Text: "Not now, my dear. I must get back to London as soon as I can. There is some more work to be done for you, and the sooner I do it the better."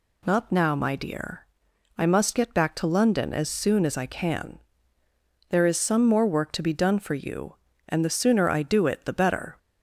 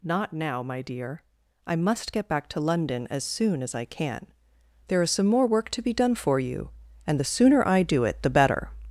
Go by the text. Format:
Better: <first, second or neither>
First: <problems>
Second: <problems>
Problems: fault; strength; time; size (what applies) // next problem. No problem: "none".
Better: first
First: none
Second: gets louder; noticeable; throughout; 5.5 dB